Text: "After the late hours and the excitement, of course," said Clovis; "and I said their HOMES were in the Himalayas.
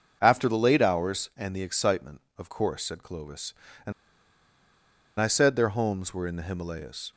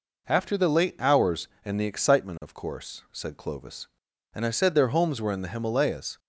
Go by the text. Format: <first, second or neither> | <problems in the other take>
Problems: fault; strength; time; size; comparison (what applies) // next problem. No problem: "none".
second | starts louder than the rest; until 1.2 s; 6.5 dB // pauses between "and" and "I"; strong; at 3.9 s; 1.2 s long